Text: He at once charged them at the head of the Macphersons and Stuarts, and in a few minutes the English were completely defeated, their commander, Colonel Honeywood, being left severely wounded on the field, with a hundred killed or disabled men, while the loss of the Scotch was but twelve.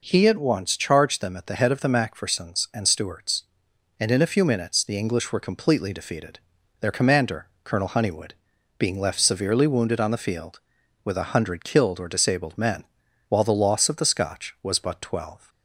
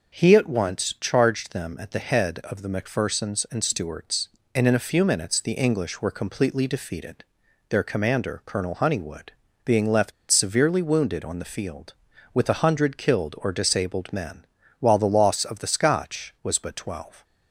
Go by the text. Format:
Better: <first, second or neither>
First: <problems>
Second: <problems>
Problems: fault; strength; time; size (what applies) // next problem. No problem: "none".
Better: first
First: none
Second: starts louder than the rest; until 1.2 s; 6 dB // pauses between "left" and "severely"; slight; at 10.1 s; 0.17 s long